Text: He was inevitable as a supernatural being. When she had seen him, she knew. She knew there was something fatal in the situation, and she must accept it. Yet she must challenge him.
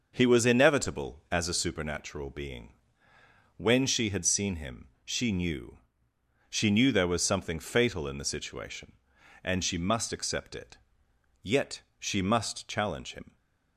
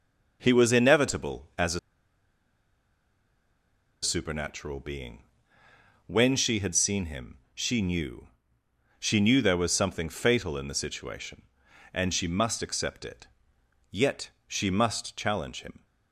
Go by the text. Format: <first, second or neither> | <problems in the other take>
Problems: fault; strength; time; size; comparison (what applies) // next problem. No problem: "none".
first | pauses between "a" and "supernatural"; strong; at 1.7 s; 2.2 s long // pauses between "Yet" and "she"; slight; at 14.2 s; 0.18 s long; slight in the first